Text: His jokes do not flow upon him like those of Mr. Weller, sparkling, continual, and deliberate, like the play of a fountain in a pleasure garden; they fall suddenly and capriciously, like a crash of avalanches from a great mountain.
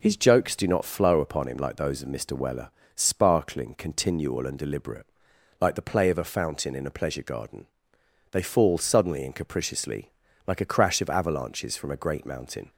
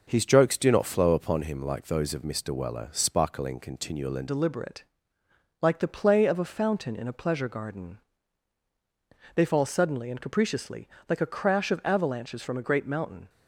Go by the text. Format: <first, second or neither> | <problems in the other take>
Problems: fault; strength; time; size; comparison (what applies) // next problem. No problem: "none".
first | changes voice at "deliberate"; from 4.2 s on; 9.0 s long